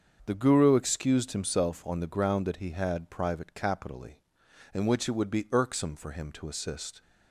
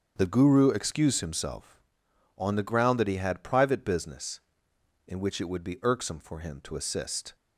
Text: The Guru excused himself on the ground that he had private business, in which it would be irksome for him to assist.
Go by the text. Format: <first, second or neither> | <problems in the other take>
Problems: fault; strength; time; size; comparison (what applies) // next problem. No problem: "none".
second | starts louder than the rest; until 1.2 s; 7 dB; strong in the second // says "capitally" for "business"; at 3.5 s